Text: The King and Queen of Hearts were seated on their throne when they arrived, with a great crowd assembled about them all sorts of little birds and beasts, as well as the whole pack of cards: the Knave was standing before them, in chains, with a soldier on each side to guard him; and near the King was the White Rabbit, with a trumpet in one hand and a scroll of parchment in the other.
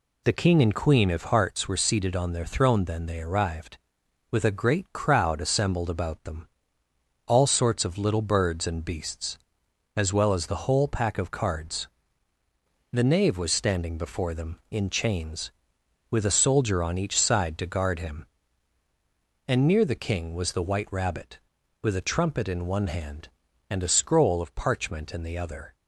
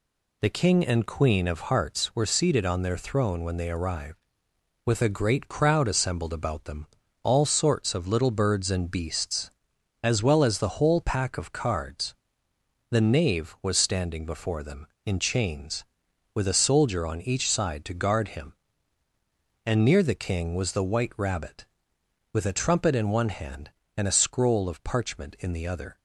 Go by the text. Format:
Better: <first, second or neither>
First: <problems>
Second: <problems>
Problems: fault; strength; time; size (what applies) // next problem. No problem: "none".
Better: second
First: says "then" for "when"; at 2.8 s // pauses between "them" and "all"; noticeable; at 6.4 s; 0.78 s long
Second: pauses between "them" and "all"; at 6.8 s; 0.38 s long